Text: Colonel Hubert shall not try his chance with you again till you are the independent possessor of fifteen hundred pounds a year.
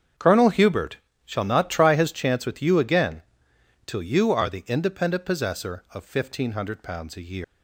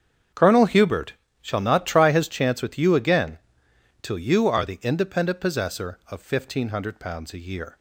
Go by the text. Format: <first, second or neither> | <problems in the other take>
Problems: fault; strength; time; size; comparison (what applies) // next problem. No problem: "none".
second | starts louder than the rest; strong; until 1.4 s; 7.5 dB; strong in the second // pauses between "Hubert" and "shall"; slight; at 0.9 s; 0.26 s long; slight in the second // pauses between "again" and "till"; noticeable; at 3.2 s; 0.63 s long; noticeable in the second // leaves "year" unfinished; at 7.4 s; 145 ms